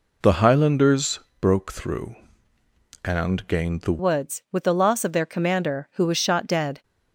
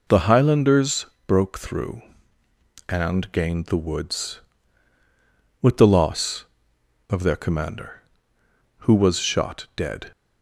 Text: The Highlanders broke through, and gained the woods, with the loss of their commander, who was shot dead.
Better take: second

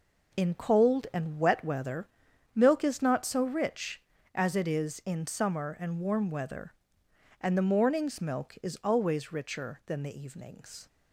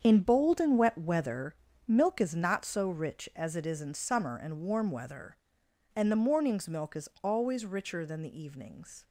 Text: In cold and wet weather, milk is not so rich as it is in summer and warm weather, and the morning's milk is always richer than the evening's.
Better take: first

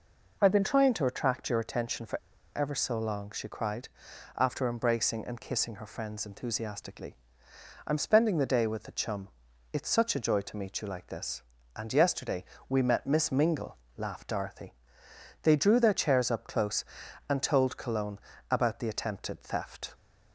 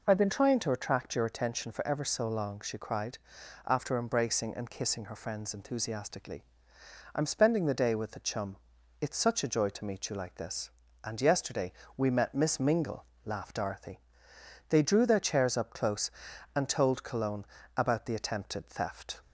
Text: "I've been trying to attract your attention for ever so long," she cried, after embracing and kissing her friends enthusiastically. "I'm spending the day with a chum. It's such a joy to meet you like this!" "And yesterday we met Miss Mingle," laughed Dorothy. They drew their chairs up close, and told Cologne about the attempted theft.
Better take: second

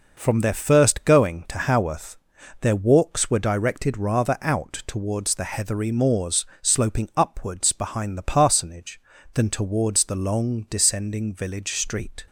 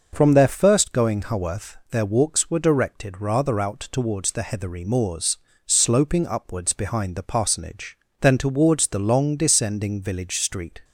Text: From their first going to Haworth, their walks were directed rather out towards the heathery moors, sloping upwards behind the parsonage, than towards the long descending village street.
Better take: first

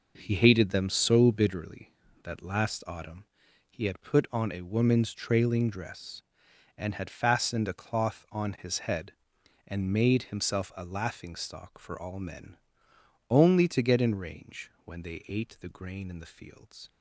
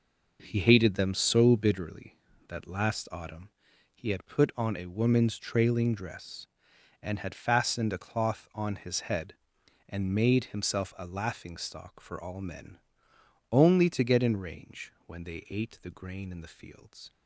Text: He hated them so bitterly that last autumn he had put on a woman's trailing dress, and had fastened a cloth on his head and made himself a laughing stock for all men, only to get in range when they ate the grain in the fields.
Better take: neither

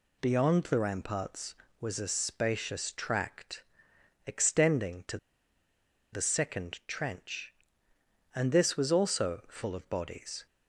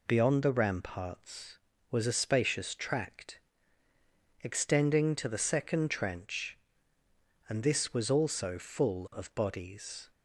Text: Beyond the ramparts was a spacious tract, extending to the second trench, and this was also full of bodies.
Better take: second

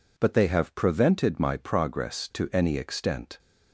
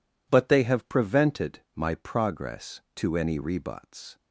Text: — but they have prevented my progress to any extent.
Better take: first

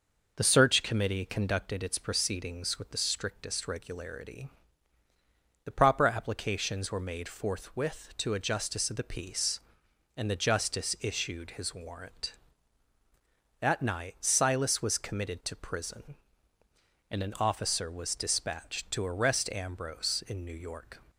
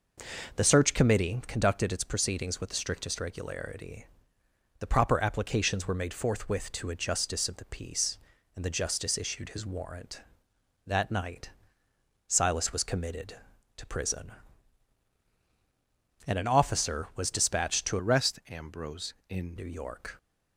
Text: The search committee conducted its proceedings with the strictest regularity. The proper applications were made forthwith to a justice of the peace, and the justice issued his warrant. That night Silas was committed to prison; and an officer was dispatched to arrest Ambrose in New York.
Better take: first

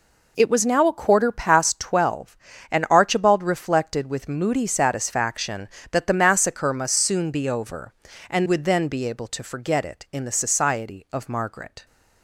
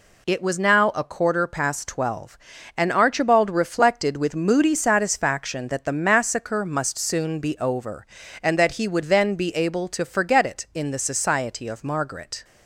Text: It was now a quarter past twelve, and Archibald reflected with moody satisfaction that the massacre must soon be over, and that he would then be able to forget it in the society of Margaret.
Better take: second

